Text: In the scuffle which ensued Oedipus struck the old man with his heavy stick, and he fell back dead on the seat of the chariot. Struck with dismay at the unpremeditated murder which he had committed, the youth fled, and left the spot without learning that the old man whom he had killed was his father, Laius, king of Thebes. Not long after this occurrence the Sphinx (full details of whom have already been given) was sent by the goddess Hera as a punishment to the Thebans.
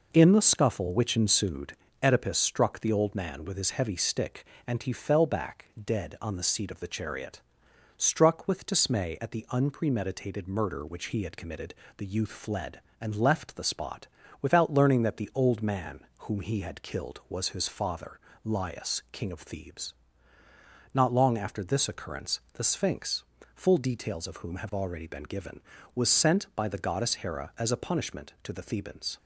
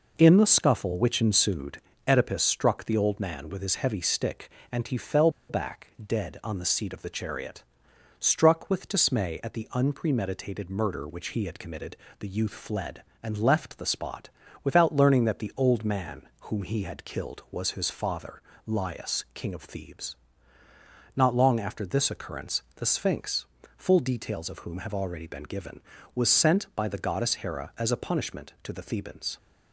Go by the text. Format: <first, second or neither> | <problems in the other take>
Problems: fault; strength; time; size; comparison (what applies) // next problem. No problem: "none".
first | pauses between "ensued" and "Oedipus"; slight; at 1.8 s; 0.26 s long; slight in the first // pauses between "fell" and "back"; slight; at 5.2 s; 0.20 s long // pauses between "spot" and "without"; slight; at 14.3 s; 0.32 s long; slight in the first // pauses between "man" and "whom"; slight; at 16.2 s; 0.18 s long; slight in the first